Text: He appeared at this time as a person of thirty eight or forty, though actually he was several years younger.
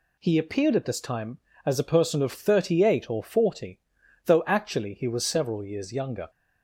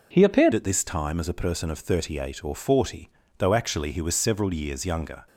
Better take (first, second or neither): first